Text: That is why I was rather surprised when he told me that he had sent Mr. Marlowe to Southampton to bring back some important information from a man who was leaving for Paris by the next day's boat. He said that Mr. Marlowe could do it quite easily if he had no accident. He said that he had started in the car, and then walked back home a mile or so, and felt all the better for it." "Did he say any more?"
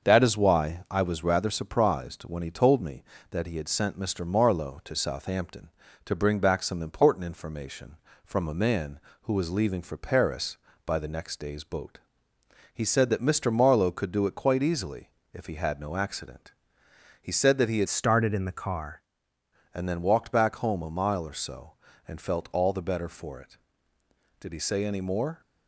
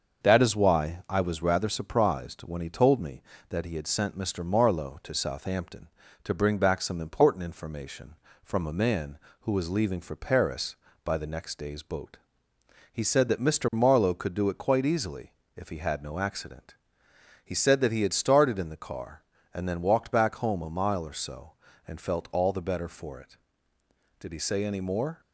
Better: second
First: starts louder than the rest; until 1.1 s; 6.5 dB // pauses between "easily" and "if"; slight; at 15.0 s; 0.24 s long // changes voice from "started" to "car"; from 17.8 to 19.0 s; 1.2 s long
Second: starts louder than the rest; until 1.2 s; 6.5 dB // pauses between "easily" and "if"; slight; at 15.3 s; 0.24 s long

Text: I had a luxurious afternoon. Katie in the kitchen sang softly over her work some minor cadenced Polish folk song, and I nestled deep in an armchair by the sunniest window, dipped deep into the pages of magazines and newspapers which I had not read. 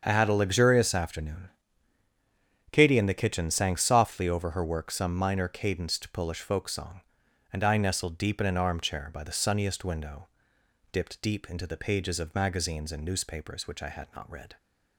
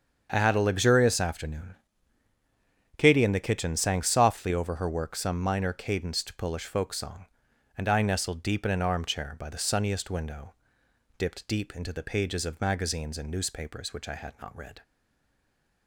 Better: first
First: starts louder than the rest; strong; until 1.0 s; 7 dB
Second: starts louder than the rest; strong; until 1.3 s; 7 dB // stays silent after the last word; from 14.8 s on; 1.0 s long

